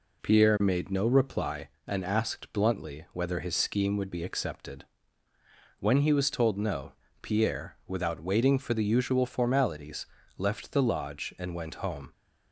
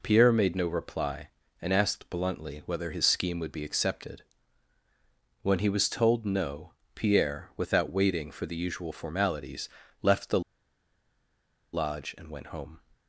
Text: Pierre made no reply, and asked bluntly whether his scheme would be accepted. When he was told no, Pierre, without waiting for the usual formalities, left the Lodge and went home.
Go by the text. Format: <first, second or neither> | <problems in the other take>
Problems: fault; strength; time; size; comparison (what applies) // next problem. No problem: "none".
first | pauses between "the" and "Lodge"; strong; at 10.4 s; 1.3 s long